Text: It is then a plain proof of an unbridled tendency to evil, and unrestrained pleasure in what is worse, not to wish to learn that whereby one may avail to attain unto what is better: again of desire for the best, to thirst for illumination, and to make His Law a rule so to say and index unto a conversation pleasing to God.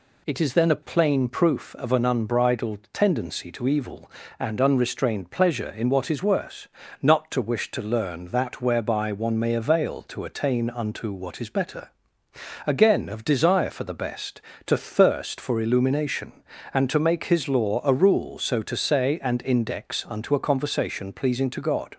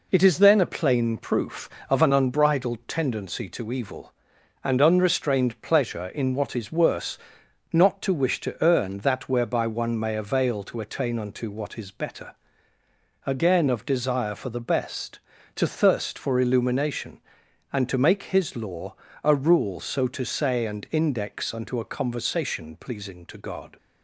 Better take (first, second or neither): first